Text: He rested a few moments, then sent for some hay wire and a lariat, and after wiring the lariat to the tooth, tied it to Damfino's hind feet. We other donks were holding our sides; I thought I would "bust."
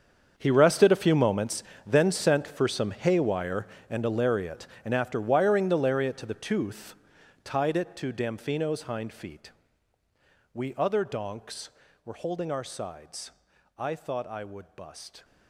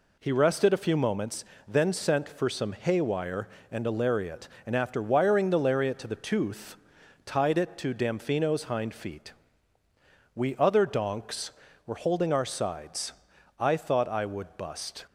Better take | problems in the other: second | gets quieter; strong; throughout; 15.5 dB

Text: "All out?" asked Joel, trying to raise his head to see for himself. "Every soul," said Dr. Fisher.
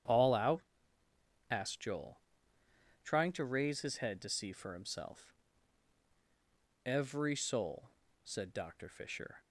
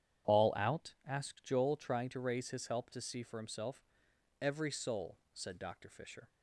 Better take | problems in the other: first | starts louder than the rest; strong; until 1.4 s; 9.5 dB; strong in the first // says "help" for "head"; at 2.6 s

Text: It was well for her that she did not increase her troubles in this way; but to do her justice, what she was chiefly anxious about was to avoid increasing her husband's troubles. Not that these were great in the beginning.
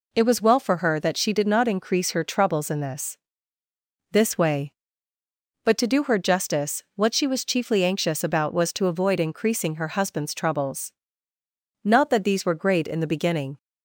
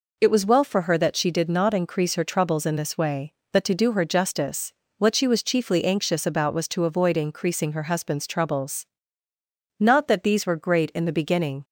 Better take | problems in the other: second | says "this" twice; at 4.1 s

